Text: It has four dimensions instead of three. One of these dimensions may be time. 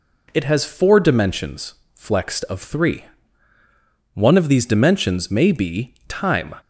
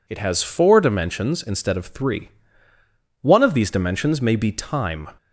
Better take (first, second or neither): second